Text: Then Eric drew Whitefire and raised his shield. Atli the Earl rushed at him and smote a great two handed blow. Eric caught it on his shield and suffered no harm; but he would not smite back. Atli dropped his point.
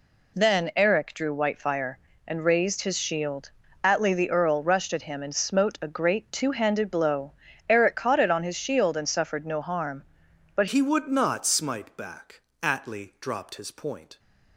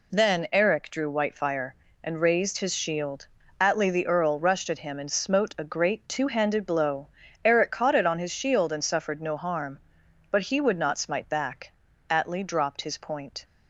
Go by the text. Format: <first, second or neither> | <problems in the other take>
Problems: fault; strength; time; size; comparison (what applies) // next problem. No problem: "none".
second | changes voice at "he"; from 10.6 s on; 3.5 s long